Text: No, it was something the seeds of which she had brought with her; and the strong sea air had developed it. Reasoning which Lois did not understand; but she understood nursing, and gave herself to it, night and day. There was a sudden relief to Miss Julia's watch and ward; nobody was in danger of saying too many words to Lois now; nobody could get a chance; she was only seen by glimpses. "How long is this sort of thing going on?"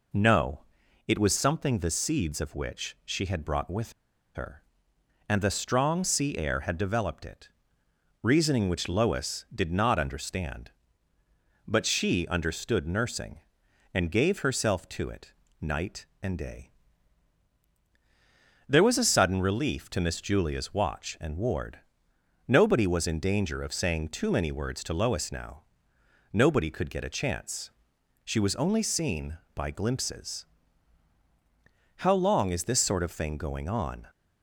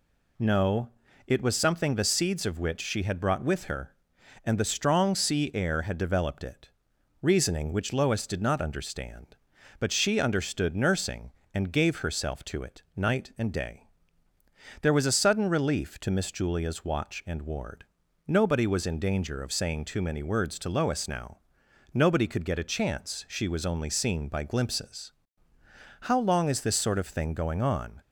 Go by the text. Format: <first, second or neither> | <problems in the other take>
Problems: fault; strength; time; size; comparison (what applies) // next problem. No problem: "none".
second | pauses between "with" and "her"; at 3.9 s; 0.42 s long